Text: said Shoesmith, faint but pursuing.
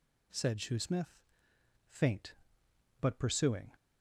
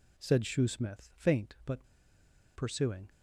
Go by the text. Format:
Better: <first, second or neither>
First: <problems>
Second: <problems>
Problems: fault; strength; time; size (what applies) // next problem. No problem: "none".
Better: first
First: none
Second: pauses between "but" and "pursuing"; noticeable; at 1.8 s; 0.70 s long